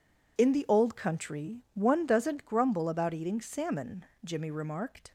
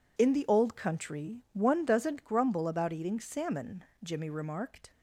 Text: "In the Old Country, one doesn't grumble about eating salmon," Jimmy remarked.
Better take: neither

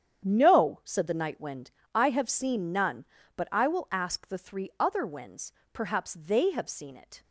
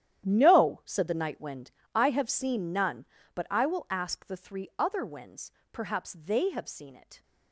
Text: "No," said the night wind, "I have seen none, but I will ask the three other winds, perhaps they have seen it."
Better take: first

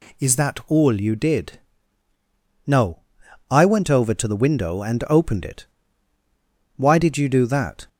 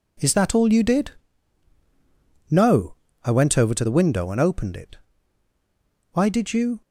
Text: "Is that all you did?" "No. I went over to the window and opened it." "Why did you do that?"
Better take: first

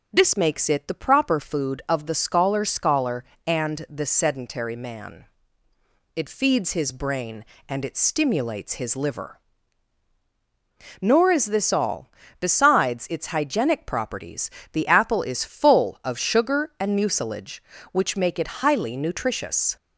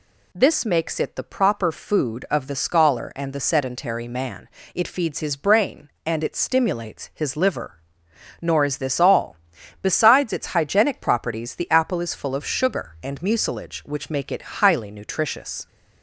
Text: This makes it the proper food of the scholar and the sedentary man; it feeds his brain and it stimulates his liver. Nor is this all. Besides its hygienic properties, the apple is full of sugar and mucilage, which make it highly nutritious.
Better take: second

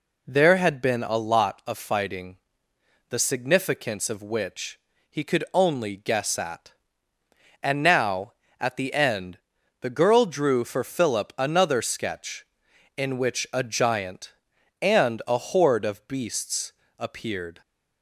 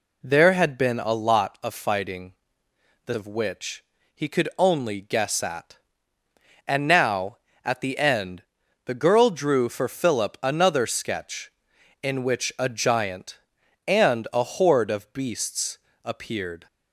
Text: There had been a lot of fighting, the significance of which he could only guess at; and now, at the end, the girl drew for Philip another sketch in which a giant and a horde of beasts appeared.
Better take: first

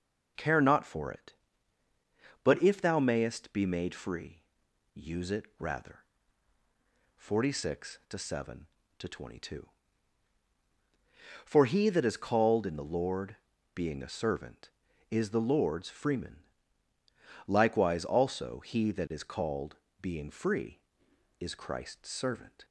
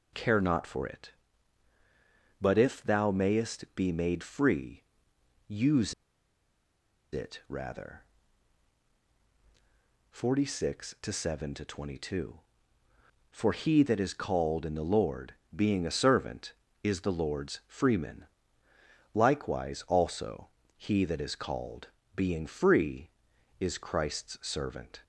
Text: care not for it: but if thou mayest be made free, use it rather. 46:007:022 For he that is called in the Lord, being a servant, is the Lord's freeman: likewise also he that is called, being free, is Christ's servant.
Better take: first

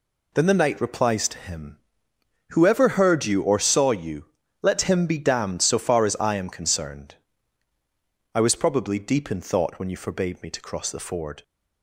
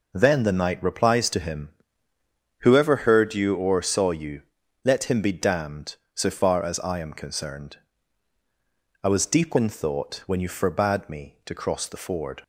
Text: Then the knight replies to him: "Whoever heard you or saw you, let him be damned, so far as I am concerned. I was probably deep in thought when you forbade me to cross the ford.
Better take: first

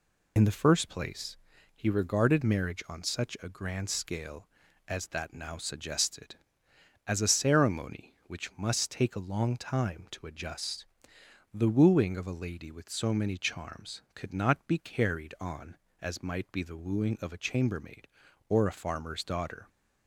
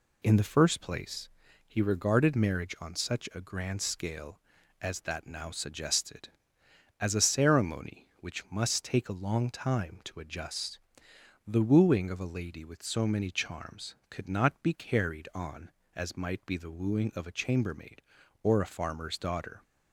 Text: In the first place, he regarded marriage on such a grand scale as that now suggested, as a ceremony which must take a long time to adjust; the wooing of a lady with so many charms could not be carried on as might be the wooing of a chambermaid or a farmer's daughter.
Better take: second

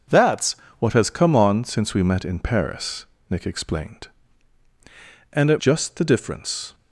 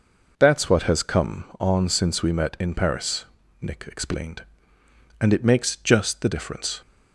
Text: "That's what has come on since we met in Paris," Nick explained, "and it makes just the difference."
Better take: second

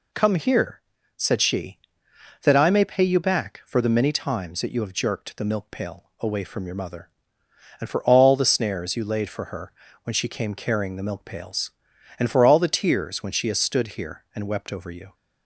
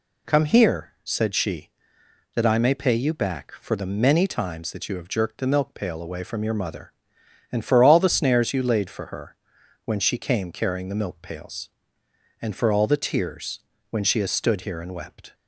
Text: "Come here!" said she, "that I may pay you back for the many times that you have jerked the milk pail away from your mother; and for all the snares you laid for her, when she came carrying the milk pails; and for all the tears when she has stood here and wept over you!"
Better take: first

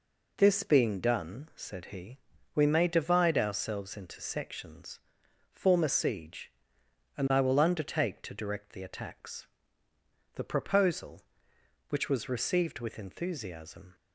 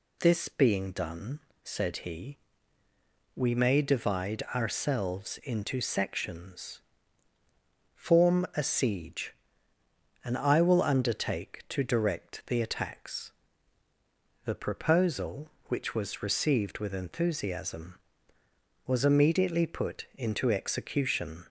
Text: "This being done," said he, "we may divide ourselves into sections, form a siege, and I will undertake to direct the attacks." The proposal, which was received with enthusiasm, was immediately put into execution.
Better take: second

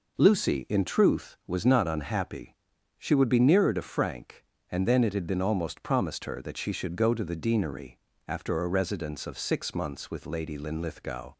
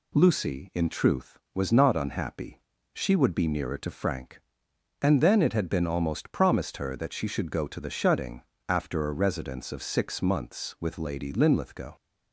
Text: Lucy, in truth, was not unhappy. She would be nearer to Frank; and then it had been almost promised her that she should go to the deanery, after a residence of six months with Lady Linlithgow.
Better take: first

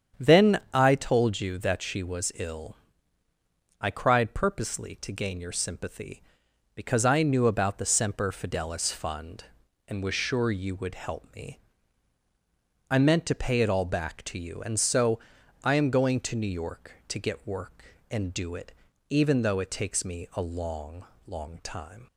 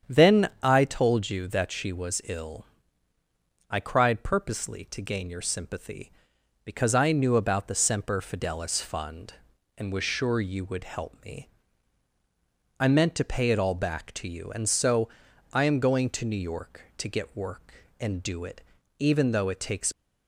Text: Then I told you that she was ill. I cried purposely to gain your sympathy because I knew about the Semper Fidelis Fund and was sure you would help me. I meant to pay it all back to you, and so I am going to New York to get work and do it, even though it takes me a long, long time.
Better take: first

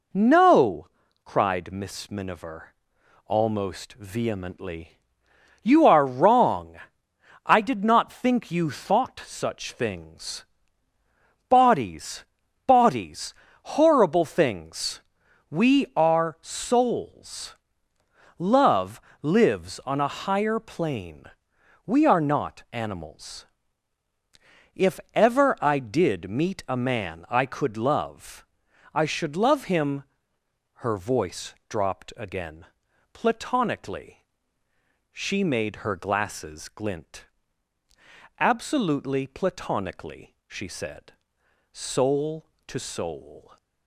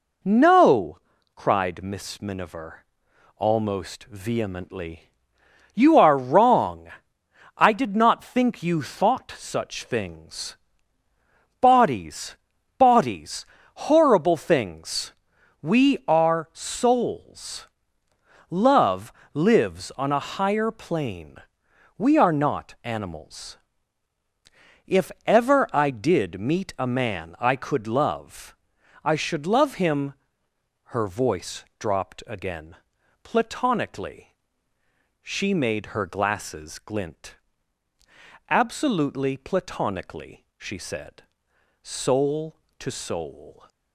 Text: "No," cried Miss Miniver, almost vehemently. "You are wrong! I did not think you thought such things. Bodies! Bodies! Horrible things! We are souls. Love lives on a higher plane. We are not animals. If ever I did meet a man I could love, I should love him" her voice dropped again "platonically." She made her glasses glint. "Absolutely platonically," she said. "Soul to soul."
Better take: neither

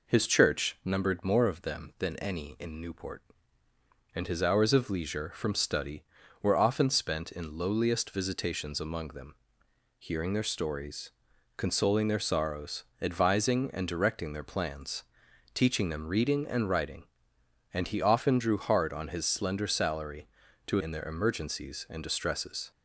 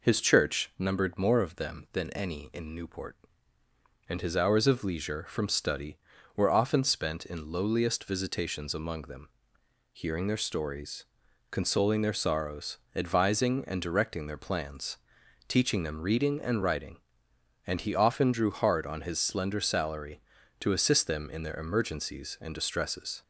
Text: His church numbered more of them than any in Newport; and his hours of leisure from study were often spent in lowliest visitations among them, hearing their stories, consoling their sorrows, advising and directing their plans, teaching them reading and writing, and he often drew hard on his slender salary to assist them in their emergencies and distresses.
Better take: second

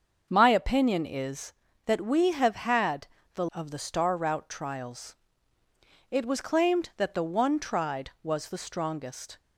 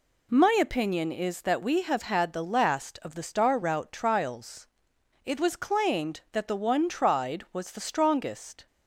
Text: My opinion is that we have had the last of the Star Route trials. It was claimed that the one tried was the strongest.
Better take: second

